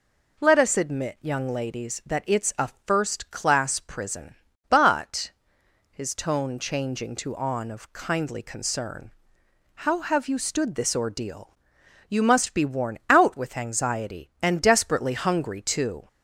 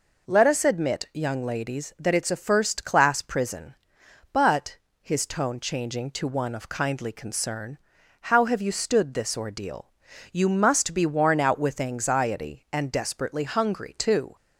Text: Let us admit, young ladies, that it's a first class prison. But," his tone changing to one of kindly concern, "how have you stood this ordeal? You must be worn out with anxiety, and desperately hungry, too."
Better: second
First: pauses between "a" and "first"; slight; at 2.6 s; 0.16 s long // says "on" for "one"; at 7.3 s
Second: none

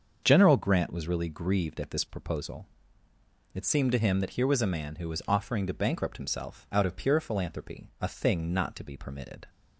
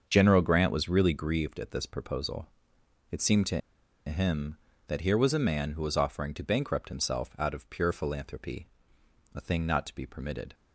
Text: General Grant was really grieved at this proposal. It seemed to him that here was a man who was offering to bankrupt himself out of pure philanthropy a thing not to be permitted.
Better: first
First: starts louder than the rest; until 1.2 s; 6.5 dB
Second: starts louder than the rest; until 1.0 s; 6.5 dB // pauses between "to" and "him"; noticeable; at 3.5 s; 0.47 s long // pauses between "philanthropy" and "a"; noticeable; at 8.6 s; 0.68 s long

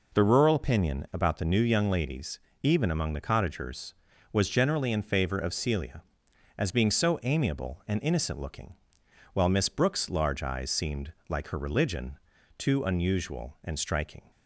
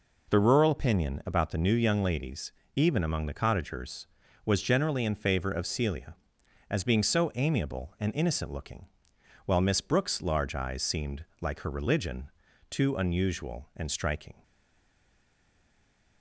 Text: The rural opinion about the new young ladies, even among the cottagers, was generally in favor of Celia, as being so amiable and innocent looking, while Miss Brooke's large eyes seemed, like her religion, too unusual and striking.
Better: first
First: none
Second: stays silent after the last word; noticeable; from 14.4 s on; 1.8 s long

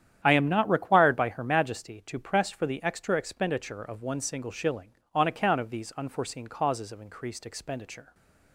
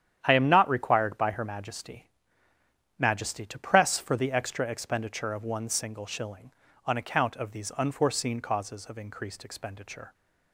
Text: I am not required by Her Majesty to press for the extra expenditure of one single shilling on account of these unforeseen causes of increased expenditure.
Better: first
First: starts louder than the rest; strong; until 1.2 s; 10 dB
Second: starts louder than the rest; strong; until 1.2 s; 9.5 dB // says "Majesty" twice; at 2.9 s

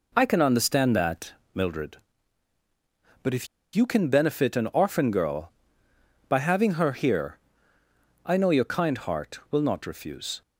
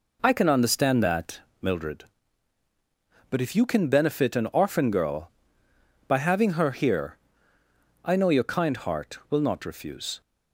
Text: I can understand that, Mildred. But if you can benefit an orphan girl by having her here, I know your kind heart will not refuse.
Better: second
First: pauses between "if" and "you"; slight; at 3.4 s; 0.28 s long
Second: none

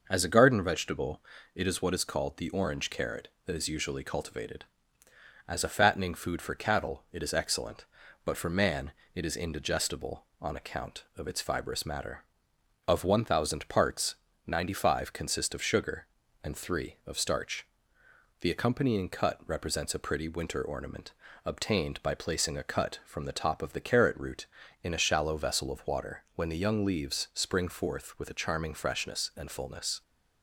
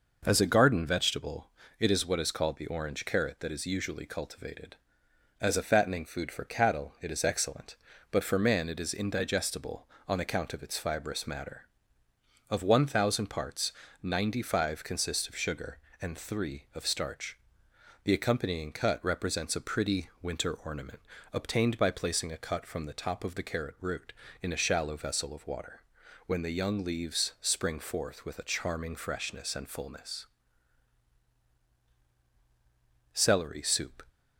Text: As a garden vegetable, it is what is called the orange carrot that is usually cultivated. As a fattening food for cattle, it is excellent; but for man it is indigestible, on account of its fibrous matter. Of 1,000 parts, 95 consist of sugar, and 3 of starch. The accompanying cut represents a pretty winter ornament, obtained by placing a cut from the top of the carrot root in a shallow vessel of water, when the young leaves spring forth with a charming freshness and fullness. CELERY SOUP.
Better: second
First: pauses between "man" and "it"; slight; at 8.9 s; 0.22 s long // stops before "CELERY SOUP"; at 30.0 s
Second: none

